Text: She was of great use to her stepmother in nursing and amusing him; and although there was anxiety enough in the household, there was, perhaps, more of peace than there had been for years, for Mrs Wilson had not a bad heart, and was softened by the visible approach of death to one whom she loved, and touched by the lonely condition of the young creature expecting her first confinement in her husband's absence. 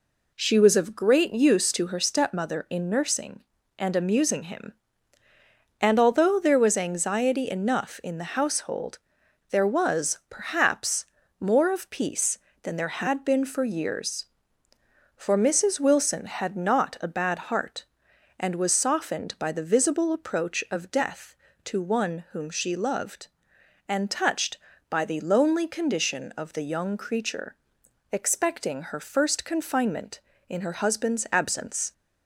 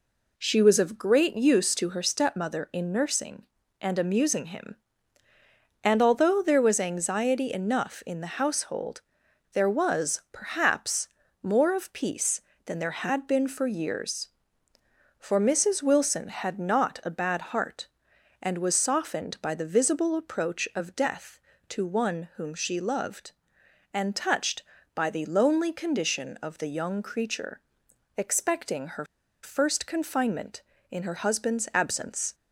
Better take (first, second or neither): first